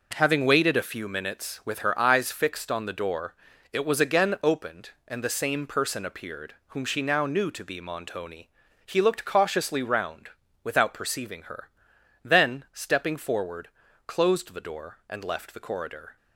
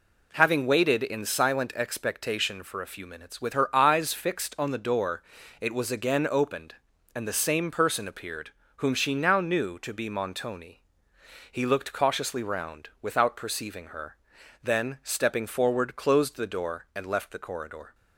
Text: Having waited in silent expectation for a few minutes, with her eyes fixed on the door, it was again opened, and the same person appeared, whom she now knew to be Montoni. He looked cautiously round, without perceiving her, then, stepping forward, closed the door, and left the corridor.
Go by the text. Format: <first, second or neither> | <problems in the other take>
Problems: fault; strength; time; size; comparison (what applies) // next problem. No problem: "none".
second | skips "in silent expectation for"; at 0.7 s